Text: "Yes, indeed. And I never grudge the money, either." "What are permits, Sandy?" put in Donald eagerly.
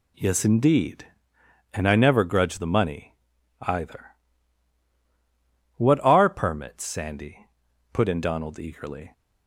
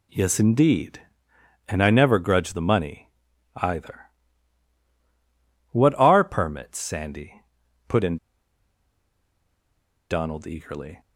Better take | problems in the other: first | pauses between "in" and "Donald"; strong; at 8.1 s; 1.9 s long

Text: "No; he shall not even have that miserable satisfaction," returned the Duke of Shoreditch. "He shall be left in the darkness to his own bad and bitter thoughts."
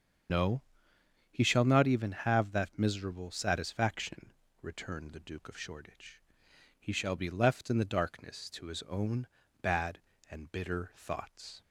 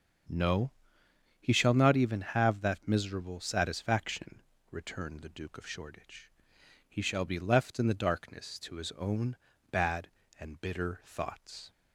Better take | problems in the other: second | loses the start of "No"; at 0.2 s; 110 ms // starts louder than the rest; strong; until 1.9 s; 7 dB; also in the second // pauses between "own" and "bad"; slight; at 9.2 s; 0.34 s long; slight in the second

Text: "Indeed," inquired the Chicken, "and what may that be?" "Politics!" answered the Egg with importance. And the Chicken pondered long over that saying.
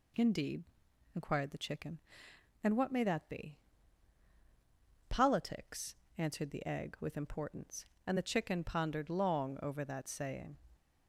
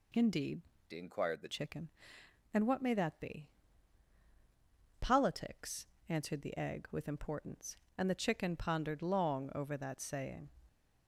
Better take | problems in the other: first | changes voice from "inquired" to "the"; from 0.9 to 1.4 s; 0.5 s long

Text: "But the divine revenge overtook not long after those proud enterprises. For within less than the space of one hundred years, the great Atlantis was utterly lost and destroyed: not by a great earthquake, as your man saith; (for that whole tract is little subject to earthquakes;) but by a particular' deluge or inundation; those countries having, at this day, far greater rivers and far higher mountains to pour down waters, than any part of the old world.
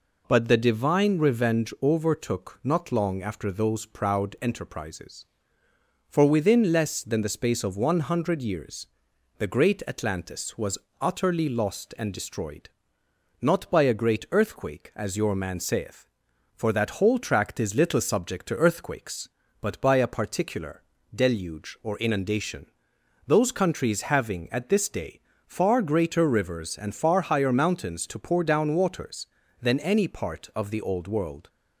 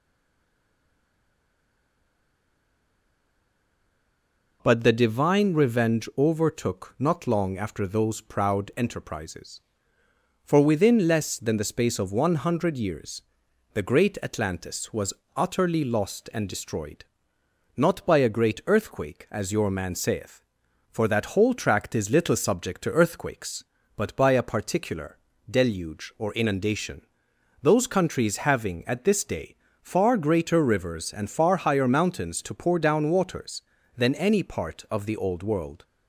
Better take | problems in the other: first | stays silent before the first word; strong; until 4.6 s; 4.6 s long // pauses between "was" and "utterly"; slight; at 15.1 s; 0.20 s long; slight in the first // pauses between "particular" and "deluge"; slight; at 25.1 s; 0.32 s long; slight in the first

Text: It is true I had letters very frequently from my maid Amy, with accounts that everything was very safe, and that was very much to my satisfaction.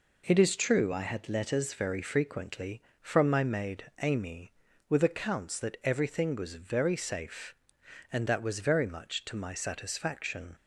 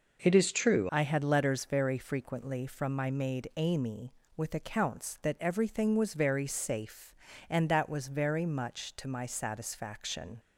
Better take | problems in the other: first | changes voice at "I"; from 0.8 s on; 9.5 s long

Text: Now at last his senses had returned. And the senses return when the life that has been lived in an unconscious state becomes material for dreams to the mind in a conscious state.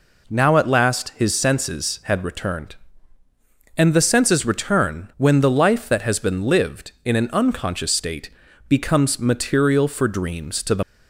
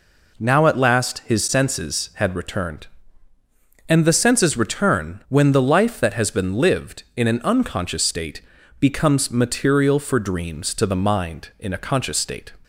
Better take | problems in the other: second | pauses between "state" and "becomes"; at 8.2 s; 0.38 s long; also in the second // stops before "mind in a conscious state"; at 10.8 s

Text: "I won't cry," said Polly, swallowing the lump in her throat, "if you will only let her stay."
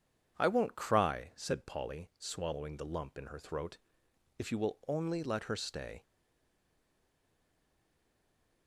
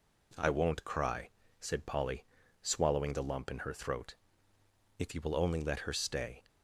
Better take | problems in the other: second | stays silent after the last word; strong; from 6.0 s on; 2.6 s long

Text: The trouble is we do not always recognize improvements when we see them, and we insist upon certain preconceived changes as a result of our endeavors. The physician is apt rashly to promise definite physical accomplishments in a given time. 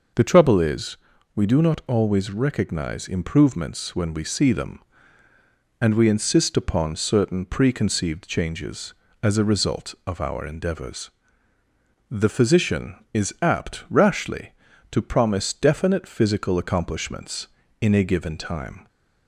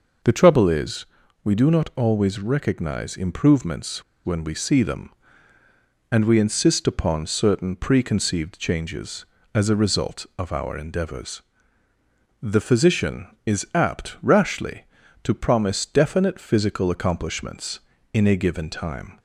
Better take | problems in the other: first | pauses between "is" and "we"; at 1.0 s; 0.38 s long; also in the first // pauses between "improvements" and "when"; slight; at 4.0 s; 0.22 s long

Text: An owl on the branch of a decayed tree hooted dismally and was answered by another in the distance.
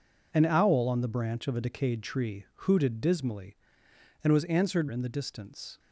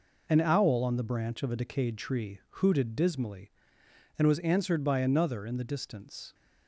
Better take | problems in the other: second | pauses between "tree" and "hooted"; slight; at 2.4 s; 0.18 s long; slight in the second // skips "by another"; at 4.8 s

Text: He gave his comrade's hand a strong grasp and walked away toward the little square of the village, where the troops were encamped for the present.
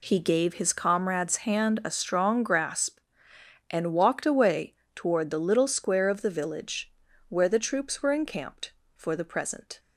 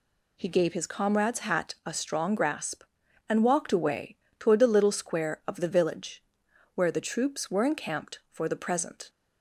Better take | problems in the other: first | says "hat" for "hand"; at 1.3 s // pauses between "away" and "toward"; slight; at 4.1 s; 0.20 s long; slight in the first

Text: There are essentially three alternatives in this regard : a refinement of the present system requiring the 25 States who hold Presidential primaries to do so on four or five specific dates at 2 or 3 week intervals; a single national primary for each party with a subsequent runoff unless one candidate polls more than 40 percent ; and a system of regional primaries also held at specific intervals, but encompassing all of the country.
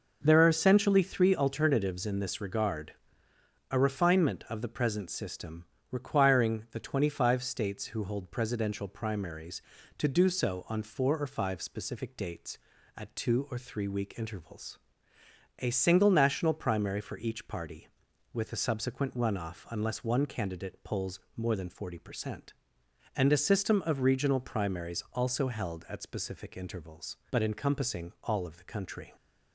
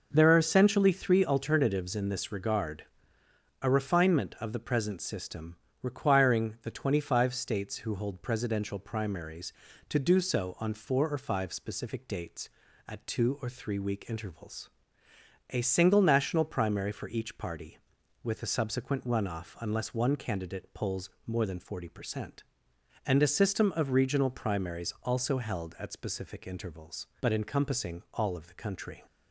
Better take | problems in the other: neither | pauses between "system" and "requiring"; slight; the same in both // pauses between "polls" and "more"; slight; the same in both

